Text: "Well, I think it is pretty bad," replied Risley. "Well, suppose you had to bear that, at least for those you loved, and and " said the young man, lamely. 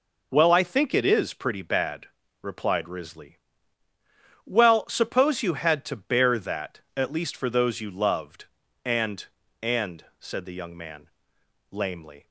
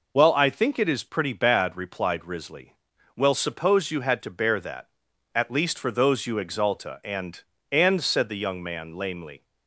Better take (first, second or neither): first